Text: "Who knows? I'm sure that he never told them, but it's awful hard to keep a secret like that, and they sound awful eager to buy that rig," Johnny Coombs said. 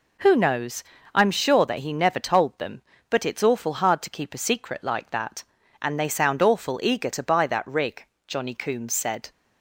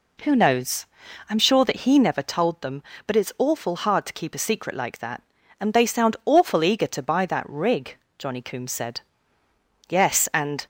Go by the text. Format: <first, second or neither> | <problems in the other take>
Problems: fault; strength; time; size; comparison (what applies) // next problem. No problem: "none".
first | goes on to say "Yes and"; noticeable; from 9.8 s on; 0.76 s long